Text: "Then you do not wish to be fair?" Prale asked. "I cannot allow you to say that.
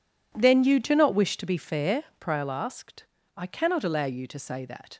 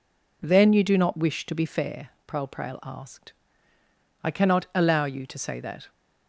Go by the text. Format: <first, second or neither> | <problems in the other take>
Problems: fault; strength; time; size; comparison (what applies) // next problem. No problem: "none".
first | says "Prale" twice; at 2.4 s